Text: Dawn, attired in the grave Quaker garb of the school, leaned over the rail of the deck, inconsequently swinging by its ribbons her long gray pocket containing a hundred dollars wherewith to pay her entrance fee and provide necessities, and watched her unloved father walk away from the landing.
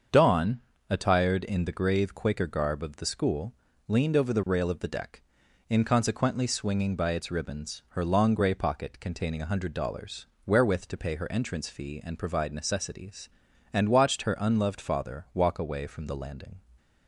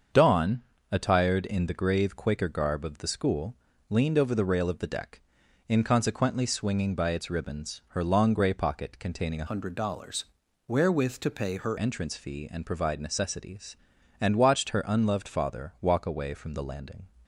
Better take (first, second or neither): first